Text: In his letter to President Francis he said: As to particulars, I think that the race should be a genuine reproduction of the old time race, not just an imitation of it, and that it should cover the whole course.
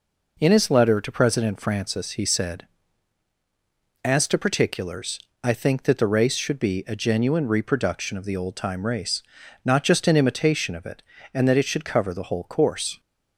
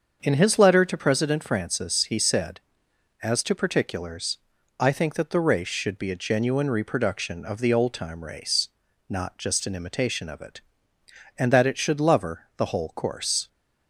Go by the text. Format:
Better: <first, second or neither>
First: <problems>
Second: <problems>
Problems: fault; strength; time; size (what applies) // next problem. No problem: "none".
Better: first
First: none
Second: starts louder than the rest; until 1.2 s; 7 dB // says "lover" for "cover"; at 11.9 s